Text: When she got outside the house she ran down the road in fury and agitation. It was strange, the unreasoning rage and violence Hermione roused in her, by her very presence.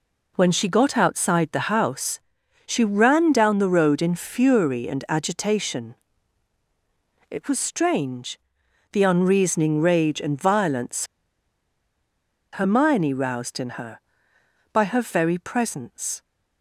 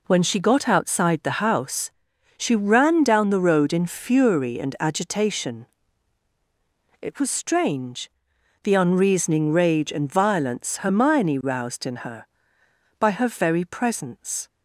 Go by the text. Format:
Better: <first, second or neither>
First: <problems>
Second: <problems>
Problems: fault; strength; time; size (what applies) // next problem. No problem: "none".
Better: second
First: pauses between "house" and "she"; noticeable; at 2.1 s; 0.48 s long // pauses between "violence" and "Hermione"; strong; at 11.0 s; 1.5 s long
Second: pauses between "house" and "she"; noticeable; at 1.8 s; 0.48 s long